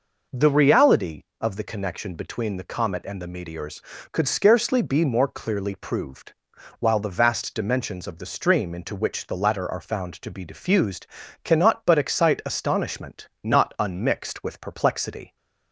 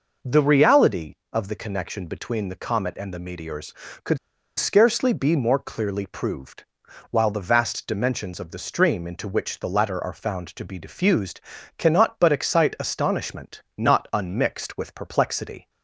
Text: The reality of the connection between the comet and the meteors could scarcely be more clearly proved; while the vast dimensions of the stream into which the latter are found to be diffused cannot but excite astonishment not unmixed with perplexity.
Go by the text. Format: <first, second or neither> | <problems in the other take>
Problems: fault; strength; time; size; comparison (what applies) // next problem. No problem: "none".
first | pauses between "could" and "scarcely"; at 4.1 s; 0.41 s long // pauses between "diffused" and "cannot"; at 11.3 s; 0.38 s long; also in the first // pauses between "astonishment" and "not"; slight; at 13.6 s; 0.16 s long; slight in the first